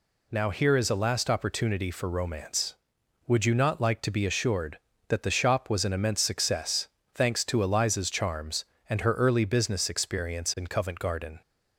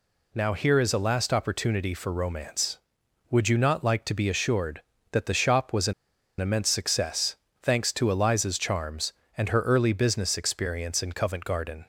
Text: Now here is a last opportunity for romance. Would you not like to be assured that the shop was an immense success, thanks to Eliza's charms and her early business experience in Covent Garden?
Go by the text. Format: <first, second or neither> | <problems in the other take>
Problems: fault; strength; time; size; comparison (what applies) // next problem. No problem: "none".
first | pauses between "an" and "immense"; noticeable; at 5.9 s; 0.47 s long